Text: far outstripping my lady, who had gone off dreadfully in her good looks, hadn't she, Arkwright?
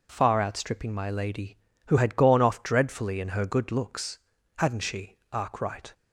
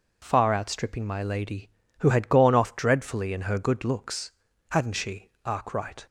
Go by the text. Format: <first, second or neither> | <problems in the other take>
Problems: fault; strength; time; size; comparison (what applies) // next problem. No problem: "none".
neither | none